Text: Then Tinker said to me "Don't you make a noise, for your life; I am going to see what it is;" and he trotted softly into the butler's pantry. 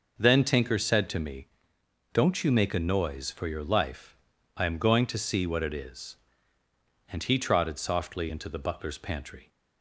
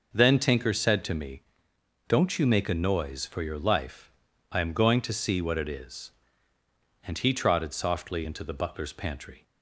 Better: neither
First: pauses between "me" and "Don't"; noticeable; at 1.4 s; 0.64 s long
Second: pauses between "me" and "Don't"; noticeable; at 1.4 s; 0.64 s long

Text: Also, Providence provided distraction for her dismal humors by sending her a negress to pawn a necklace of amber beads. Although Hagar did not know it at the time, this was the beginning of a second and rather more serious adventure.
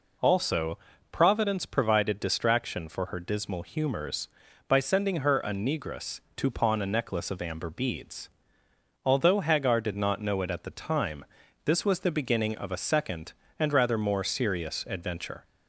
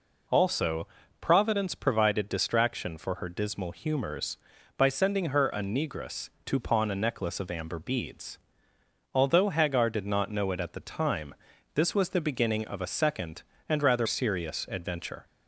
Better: first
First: none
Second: skips "more"; at 14.0 s

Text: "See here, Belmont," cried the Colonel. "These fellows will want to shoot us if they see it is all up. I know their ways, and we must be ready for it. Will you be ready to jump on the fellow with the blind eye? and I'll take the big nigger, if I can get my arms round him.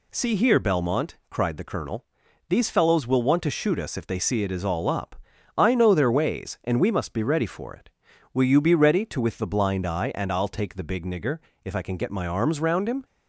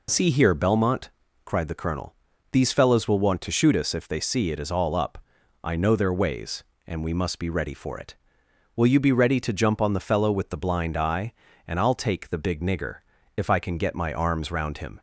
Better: second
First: skips "jump on the fellow"; at 9.2 s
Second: none

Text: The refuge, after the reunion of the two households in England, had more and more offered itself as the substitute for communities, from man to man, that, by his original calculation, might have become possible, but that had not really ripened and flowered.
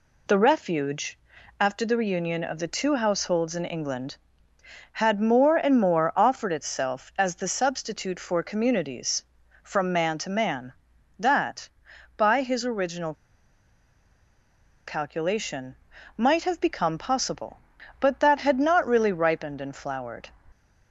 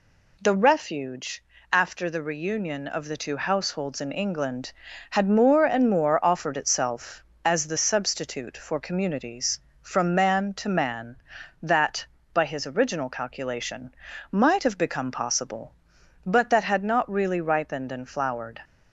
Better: second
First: pauses between "original" and "calculation"; strong; at 13.1 s; 1.7 s long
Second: none

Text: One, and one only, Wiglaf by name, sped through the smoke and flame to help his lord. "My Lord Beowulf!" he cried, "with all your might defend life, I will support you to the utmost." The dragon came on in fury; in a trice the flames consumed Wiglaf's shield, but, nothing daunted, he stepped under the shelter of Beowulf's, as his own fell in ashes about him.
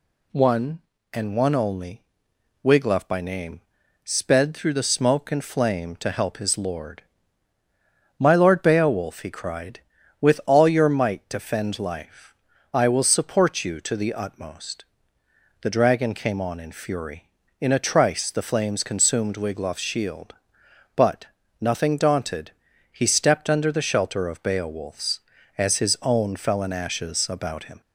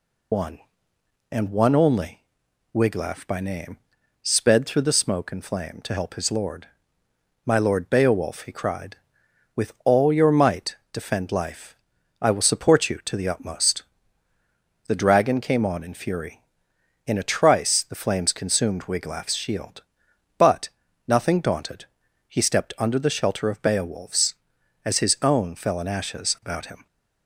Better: first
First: none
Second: loses the start of "One"; at 0.3 s; 50 ms // pauses between "might" and "defend"; slight; at 10.7 s; 0.16 s long

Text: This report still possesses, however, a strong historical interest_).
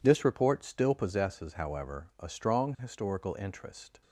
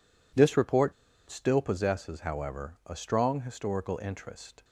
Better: first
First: none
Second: pauses between "report" and "still"; at 0.9 s; 0.36 s long

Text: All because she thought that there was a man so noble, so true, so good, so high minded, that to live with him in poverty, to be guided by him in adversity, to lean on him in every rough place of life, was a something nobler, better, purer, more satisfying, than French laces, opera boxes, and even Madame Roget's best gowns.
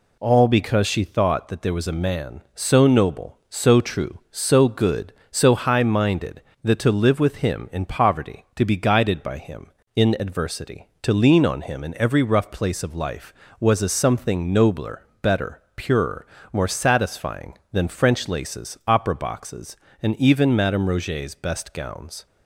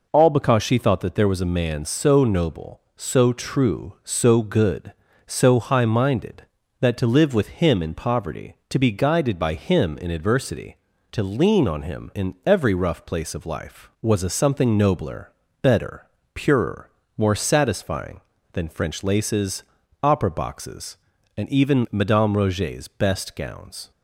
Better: neither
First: none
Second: none

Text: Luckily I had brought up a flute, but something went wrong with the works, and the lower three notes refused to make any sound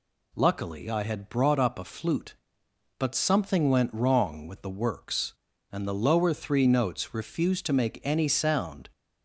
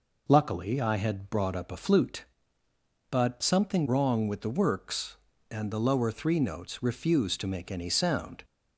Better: first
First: none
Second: skips "went"; at 3.8 s

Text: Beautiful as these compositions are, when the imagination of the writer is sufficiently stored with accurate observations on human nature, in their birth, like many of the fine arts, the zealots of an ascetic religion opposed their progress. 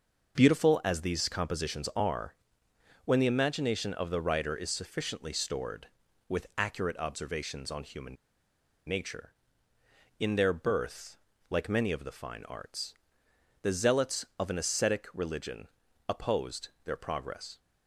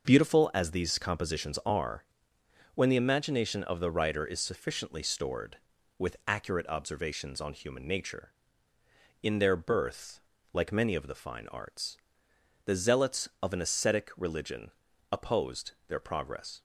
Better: second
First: pauses between "human" and "nature"; noticeable; at 8.1 s; 0.73 s long // pauses between "religion" and "opposed"; at 15.6 s; 0.40 s long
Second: pauses between "religion" and "opposed"; at 14.7 s; 0.40 s long

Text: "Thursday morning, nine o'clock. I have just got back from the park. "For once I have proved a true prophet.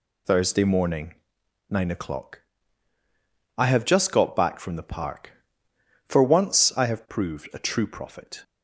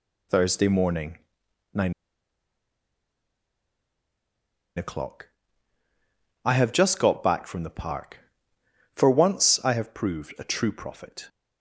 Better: first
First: none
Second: pauses between "nine" and "o'clock"; strong; at 1.9 s; 2.8 s long

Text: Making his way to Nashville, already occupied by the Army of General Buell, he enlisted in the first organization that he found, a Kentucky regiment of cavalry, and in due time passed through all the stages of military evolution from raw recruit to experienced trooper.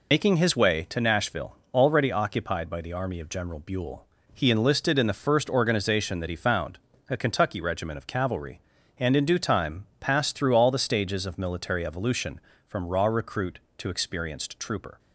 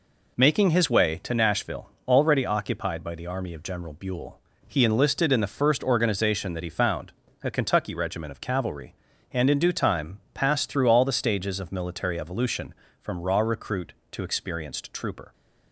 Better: second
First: loses the start of "Making"; at 0.1 s; 85 ms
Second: none

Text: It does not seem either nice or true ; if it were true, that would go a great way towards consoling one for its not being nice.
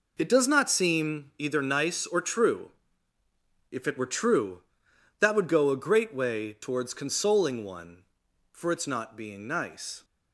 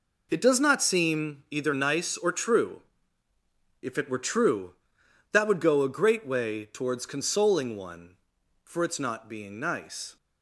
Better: neither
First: none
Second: none

